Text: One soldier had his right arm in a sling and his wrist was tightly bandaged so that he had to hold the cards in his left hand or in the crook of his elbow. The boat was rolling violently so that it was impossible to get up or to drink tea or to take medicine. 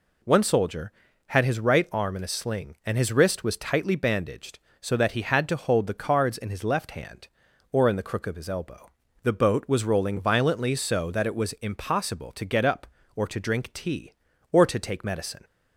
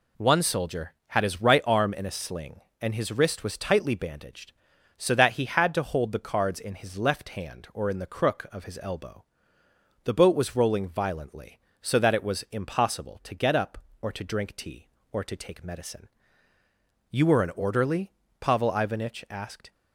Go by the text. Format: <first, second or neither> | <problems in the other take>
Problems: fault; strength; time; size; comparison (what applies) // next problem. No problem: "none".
first | goes on to say "You were an orderly Pavel Ivanich asked"; strong; from 17.1 s on; 2.6 s long